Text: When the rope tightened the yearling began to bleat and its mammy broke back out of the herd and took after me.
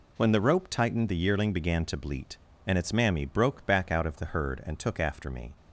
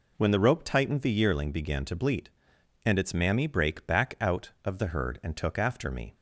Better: first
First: none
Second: says "brake" for "broke"; at 3.4 s

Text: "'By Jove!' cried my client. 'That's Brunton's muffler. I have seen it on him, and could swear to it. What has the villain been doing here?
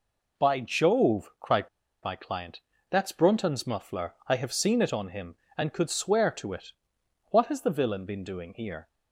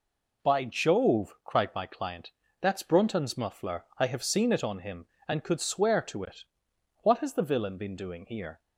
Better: second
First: pauses between "cried" and "my"; slight; at 1.6 s; 0.34 s long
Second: none

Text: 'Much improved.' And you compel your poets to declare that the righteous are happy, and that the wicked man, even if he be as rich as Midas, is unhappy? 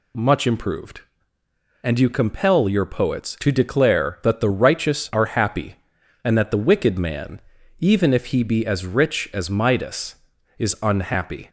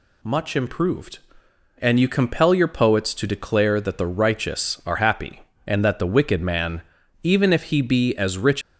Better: first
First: none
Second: stops before "as Midas is unhappy"; at 8.6 s

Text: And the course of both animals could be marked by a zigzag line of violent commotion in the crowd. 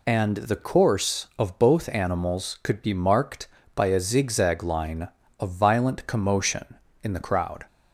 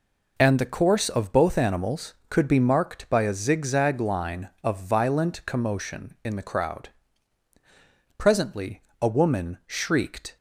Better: first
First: none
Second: goes on to say "Presently a woman shrieked"; strong; from 8.1 s on; 2.1 s long

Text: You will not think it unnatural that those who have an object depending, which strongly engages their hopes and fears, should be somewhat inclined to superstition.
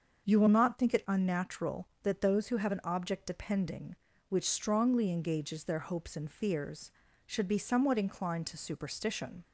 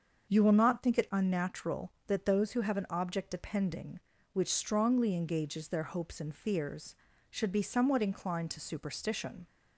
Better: neither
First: starts louder than the rest; until 1.3 s; 6.5 dB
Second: starts louder than the rest; until 1.3 s; 6.5 dB

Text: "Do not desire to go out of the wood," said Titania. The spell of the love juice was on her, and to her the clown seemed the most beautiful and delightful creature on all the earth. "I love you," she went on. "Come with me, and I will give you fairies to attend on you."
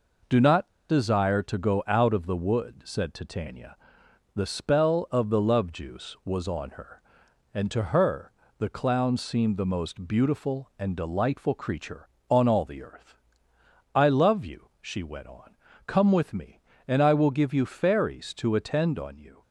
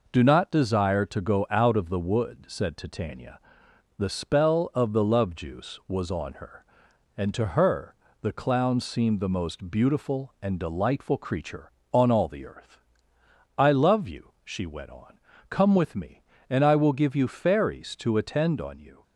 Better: second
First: pauses between "not" and "desire"; slight; at 0.6 s; 0.21 s long // pauses between "her" and "the"; slight; at 8.3 s; 0.26 s long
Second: pauses between "her" and "the"; slight; at 7.9 s; 0.26 s long

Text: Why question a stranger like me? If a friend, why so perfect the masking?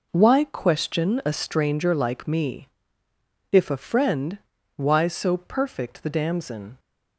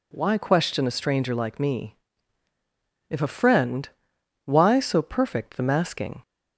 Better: second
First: says "damson" for "masking"; at 6.0 s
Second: none

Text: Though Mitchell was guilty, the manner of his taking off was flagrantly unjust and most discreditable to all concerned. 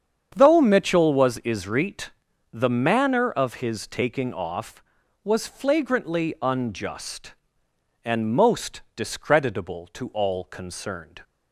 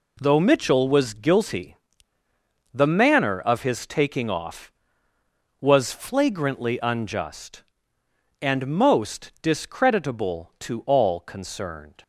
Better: second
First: starts louder than the rest; strong; until 1.3 s; 8 dB // says "isrit" for "guilty"; at 1.3 s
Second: none

